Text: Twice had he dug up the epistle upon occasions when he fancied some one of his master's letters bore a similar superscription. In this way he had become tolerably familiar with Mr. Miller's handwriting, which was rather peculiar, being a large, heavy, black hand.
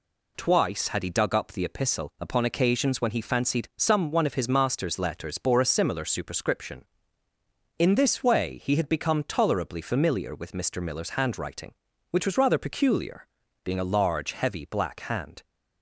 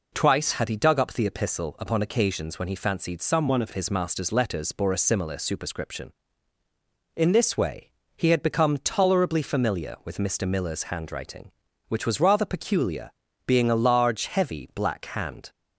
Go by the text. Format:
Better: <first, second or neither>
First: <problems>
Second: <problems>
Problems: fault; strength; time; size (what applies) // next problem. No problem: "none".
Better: first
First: none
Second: changes voice from "one" to "of"; from 3.4 to 3.6 s; 0.2 s long // pauses between "way" and "he"; slight; at 7.8 s; 0.26 s long